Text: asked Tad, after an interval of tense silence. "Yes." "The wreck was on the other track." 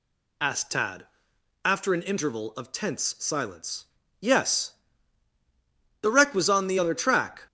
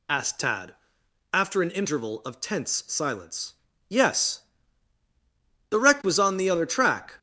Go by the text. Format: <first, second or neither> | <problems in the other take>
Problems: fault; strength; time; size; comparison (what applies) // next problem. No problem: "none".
neither | none